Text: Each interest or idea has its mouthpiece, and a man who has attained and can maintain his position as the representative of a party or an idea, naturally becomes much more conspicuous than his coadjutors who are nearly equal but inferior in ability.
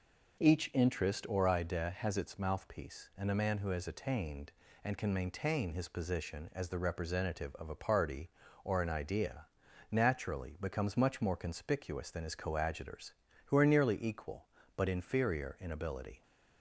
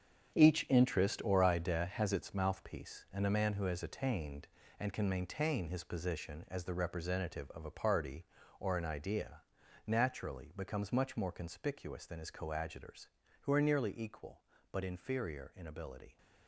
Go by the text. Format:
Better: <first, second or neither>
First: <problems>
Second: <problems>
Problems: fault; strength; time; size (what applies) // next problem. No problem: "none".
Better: first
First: none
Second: gets quieter; strong; throughout; 10.5 dB